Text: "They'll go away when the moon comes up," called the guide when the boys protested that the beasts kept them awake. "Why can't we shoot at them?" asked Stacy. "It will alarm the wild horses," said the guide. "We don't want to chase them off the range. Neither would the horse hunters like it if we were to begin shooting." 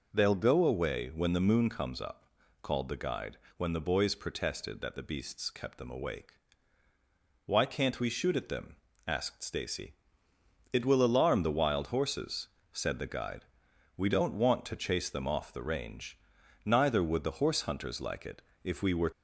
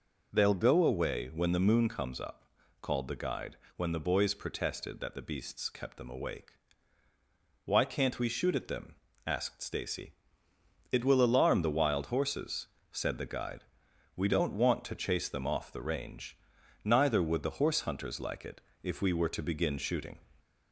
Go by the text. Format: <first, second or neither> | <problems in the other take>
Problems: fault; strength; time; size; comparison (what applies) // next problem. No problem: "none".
second | pauses between "guide" and "when"; slight; at 3.3 s; 0.18 s long; slight in the second // pauses between "it" and "if"; slight; at 18.4 s; 0.22 s long; slight in the second // stops before "to begin shooting"; at 19.1 s